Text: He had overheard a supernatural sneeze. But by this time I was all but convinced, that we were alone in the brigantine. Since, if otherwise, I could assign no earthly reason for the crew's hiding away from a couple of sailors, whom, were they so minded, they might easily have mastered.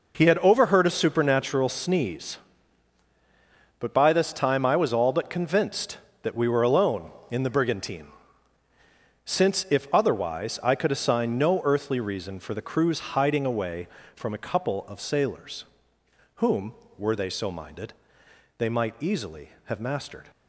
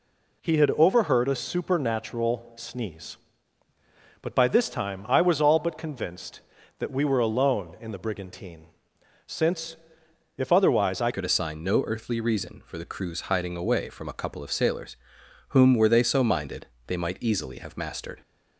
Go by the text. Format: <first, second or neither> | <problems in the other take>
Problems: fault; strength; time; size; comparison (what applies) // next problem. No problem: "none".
first | changes voice at "could"; from 11.1 s on; 7.1 s long